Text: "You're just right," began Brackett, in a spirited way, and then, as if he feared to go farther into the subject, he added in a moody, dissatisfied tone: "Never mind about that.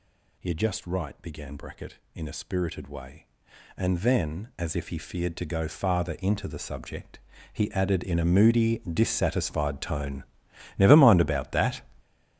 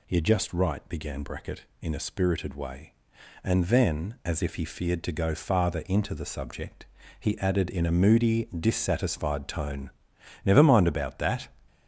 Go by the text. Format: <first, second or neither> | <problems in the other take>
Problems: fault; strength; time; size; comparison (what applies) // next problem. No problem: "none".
second | gets louder; strong; throughout; 13 dB